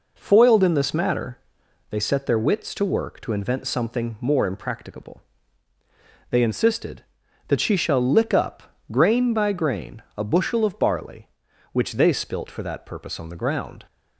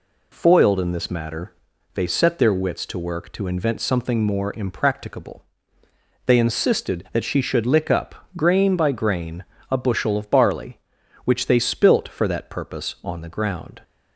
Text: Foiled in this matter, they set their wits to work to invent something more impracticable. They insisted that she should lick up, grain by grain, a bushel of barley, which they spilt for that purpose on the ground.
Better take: second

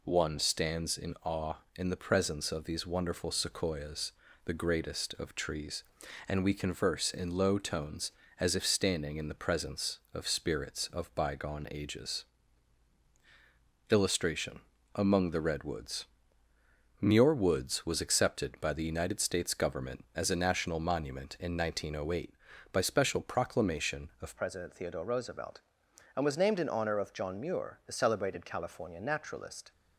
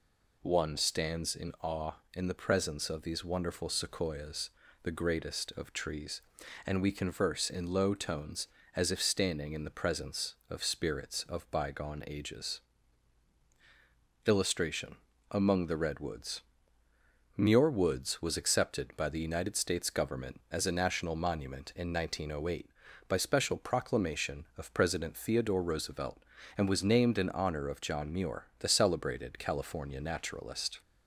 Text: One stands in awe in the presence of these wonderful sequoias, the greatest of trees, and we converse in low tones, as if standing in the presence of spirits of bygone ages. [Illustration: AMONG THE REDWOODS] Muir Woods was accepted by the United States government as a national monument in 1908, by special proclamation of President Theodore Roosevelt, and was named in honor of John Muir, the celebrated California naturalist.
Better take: second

